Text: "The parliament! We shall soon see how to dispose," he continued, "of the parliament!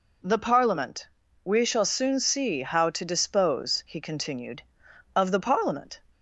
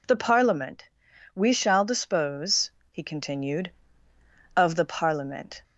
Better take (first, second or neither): first